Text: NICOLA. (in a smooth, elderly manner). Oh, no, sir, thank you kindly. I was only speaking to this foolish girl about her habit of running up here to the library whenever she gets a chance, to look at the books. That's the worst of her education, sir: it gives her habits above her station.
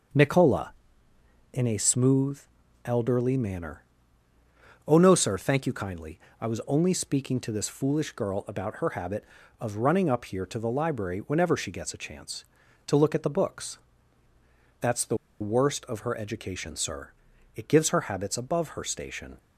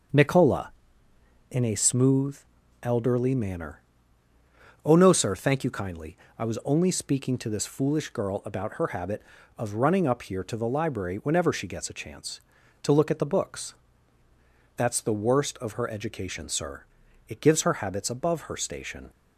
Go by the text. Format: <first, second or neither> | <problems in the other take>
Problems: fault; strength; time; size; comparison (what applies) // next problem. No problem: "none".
second | starts louder than the rest; until 1.9 s; 6.5 dB; also in the second // pauses between "the" and "worst"; slight; at 15.1 s; 0.24 s long